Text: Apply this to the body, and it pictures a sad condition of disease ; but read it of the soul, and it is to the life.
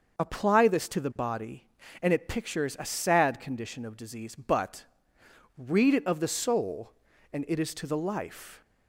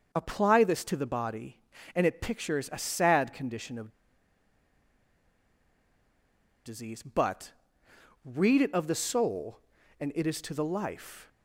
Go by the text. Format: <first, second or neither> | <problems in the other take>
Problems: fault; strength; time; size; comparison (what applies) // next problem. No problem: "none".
first | starts louder than the rest; until 1.1 s; 6 dB; also in the first // pauses between "of" and "disease"; strong; at 3.8 s; 2.7 s long // pauses between "but" and "read"; noticeable; at 7.5 s; 0.72 s long; noticeable in the first